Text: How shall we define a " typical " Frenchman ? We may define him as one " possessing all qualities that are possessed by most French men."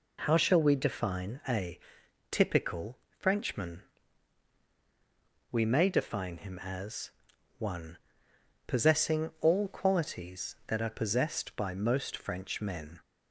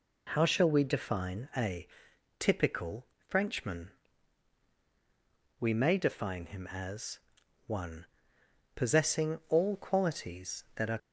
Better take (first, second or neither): first